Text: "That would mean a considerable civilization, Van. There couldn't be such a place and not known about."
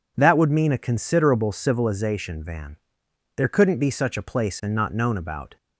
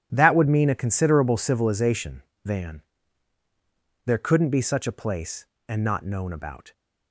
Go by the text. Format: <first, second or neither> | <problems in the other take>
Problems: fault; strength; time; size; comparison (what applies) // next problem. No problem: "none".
neither | none